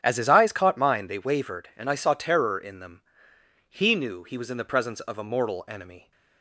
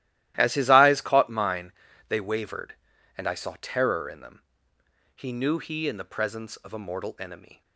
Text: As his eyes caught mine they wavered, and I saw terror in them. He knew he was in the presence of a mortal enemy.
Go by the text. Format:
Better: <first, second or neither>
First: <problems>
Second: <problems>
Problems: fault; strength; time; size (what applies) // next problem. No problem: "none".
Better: first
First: starts louder than the rest; strong; until 1.0 s; 9 dB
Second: starts louder than the rest; strong; until 1.3 s; 14.5 dB // pauses between "mine" and "they"; at 1.7 s; 0.38 s long // skips "was"; at 5.8 s